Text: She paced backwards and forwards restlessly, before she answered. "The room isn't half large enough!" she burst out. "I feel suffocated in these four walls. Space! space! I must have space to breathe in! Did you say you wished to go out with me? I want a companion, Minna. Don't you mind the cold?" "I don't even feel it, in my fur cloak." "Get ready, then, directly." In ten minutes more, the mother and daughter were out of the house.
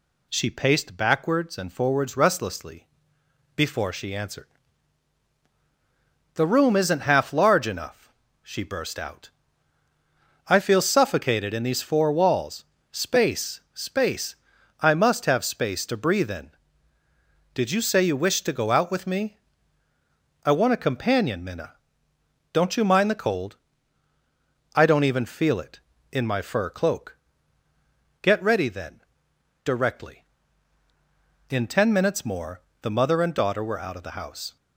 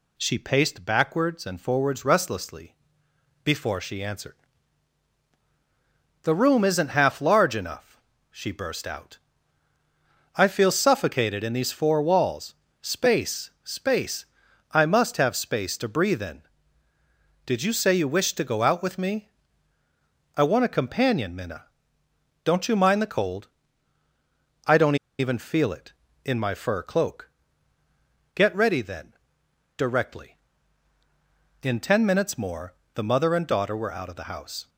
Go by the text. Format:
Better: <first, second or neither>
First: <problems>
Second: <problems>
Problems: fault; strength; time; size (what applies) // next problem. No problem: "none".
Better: first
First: none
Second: pauses between "don't" and "even"; slight; at 24.9 s; 0.23 s long